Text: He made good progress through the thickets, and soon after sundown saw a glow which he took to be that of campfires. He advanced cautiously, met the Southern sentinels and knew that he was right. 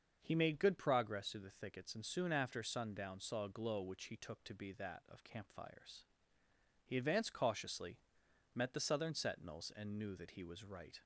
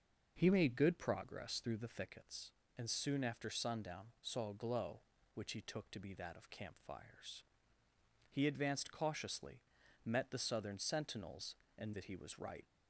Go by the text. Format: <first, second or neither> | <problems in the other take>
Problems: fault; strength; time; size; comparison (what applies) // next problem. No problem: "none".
first | starts louder than the rest; noticeable; until 1.3 s; 6 dB; also in the first // skips "knew"; at 11.9 s